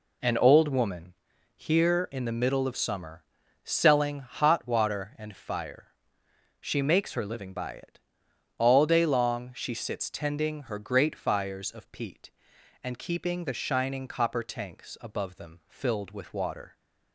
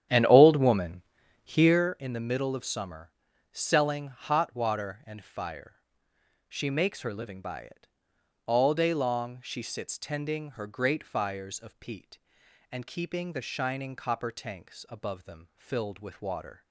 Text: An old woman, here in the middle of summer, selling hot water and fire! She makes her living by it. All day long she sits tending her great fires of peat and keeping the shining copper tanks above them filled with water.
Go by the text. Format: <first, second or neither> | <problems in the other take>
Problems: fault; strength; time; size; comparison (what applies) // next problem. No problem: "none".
first | starts louder than the rest; strong; until 1.9 s; 10 dB